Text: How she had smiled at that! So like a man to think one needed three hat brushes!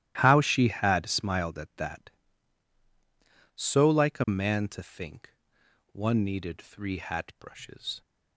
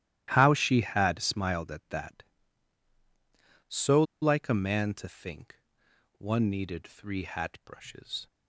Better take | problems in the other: first | starts louder than the rest; strong; until 1.3 s; 13 dB; strong in the first // pauses between "So" and "like"; slight; at 4.0 s; 0.18 s long // pauses between "think" and "one"; noticeable; at 5.5 s; 0.64 s long; noticeable in the first

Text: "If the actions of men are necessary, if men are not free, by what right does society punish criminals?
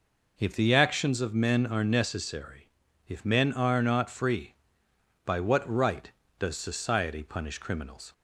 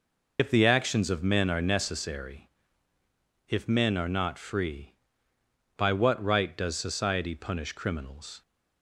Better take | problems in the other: first | loses the start of "If"; at 0.3 s; 90 ms

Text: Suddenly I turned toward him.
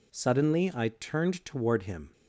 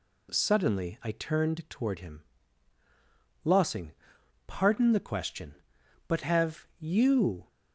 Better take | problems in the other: first | goes on to say "Lossing pardon the question but have you"; strong; from 3.4 s on; 4.0 s long

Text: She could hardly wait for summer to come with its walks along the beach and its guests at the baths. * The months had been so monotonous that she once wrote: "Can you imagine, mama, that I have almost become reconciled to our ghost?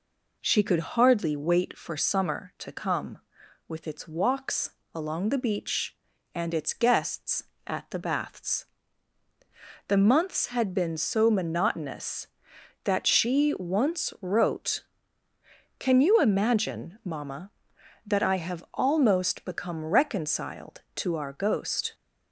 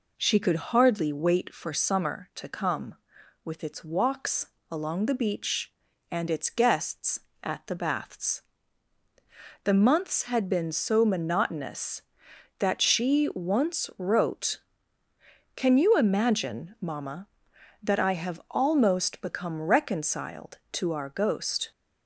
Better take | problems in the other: neither | pauses between "walks" and "along"; slight; the same in both

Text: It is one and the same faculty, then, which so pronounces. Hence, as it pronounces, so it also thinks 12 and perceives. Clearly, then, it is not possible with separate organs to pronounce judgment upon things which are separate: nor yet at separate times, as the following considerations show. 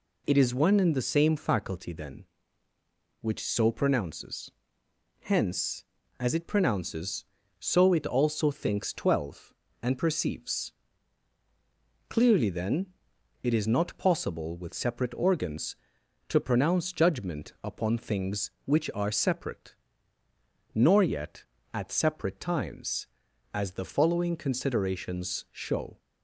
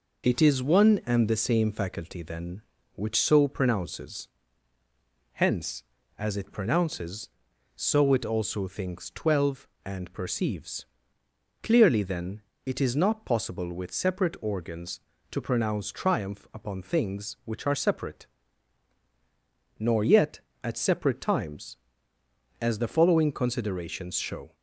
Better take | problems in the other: first | says "triumph" for "judgment"; at 15.9 s

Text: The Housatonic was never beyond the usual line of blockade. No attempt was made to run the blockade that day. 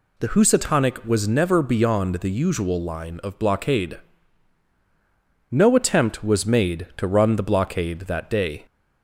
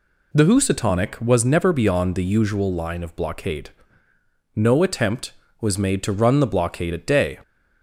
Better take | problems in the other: first | says "at" for "that"; at 6.9 s

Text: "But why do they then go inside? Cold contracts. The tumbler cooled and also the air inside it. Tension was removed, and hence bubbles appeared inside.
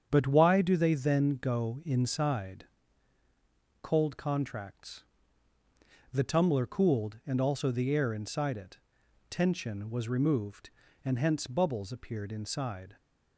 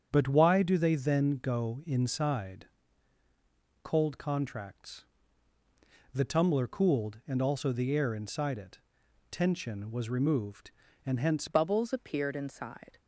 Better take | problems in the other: first | starts louder than the rest; strong; until 1.1 s; 8 dB; strong in the first // changes voice at "bubbles"; from 11.4 s on; 1.5 s long

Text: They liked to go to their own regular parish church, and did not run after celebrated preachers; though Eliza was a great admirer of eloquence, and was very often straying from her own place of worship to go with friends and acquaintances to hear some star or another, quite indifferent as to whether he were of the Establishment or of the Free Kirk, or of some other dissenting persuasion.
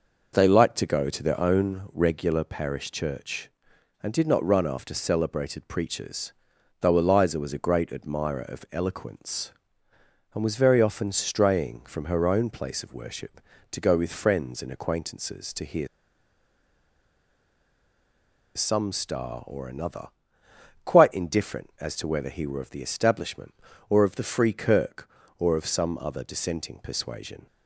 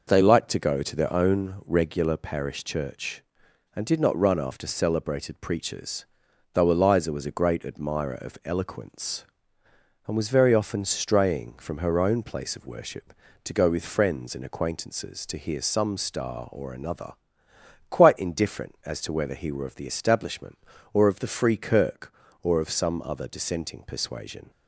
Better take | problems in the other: second | pauses between "hear" and "some"; strong; at 15.8 s; 2.6 s long

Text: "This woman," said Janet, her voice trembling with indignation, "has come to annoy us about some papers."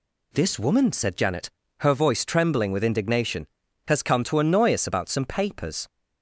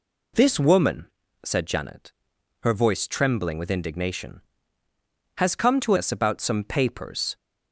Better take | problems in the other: first | skips "annoy"; at 5.9 s

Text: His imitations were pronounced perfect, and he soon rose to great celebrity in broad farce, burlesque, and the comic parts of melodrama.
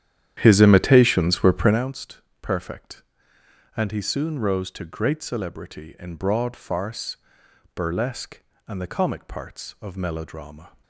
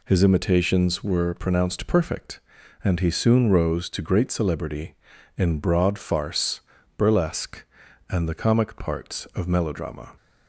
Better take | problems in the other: second | starts louder than the rest; strong; until 1.8 s; 10.5 dB // pauses between "pronounced" and "perfect"; slight; at 2.2 s; 0.22 s long

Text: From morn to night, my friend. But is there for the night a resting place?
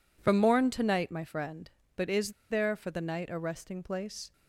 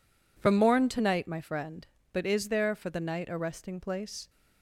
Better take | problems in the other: second | pauses between "is" and "there"; slight; at 2.3 s; 0.17 s long

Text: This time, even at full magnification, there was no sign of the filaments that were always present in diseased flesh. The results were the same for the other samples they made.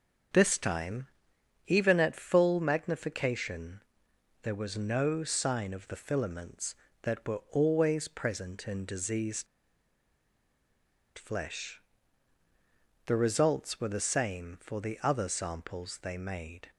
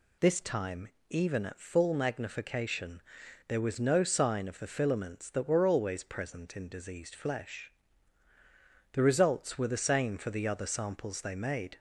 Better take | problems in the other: second | starts louder than the rest; until 1.9 s; 7 dB // pauses between "diseased" and "flesh"; strong; at 9.4 s; 1.7 s long

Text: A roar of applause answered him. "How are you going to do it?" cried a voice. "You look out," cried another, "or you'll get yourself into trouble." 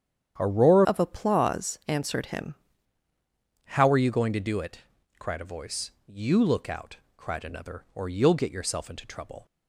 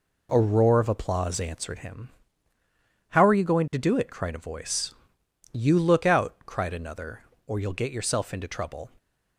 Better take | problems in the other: second | starts louder than the rest; strong; until 1.4 s; 9 dB // changes voice from "of" to "him"; from 0.8 to 2.5 s; 1.7 s long

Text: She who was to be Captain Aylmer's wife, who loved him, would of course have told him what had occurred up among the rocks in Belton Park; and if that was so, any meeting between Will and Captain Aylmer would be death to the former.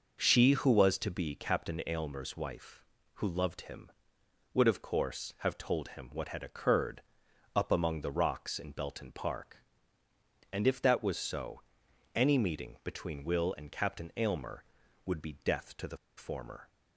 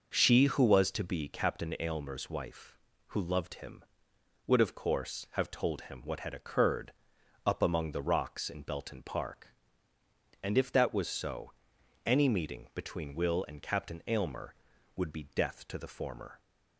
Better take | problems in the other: second | pauses between "occurred" and "up"; noticeable; at 7.0 s; 0.52 s long; noticeable in the second // pauses between "the" and "former"; slight; at 15.9 s; 0.20 s long

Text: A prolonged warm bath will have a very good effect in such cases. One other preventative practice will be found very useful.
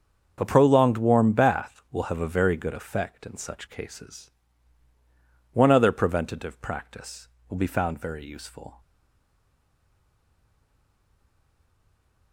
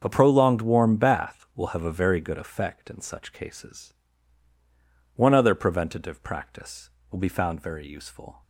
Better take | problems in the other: second | starts louder than the rest; until 1.4 s; 7 dB; also in the second // stays silent after the last word; strong; from 8.8 s on; 3.5 s long

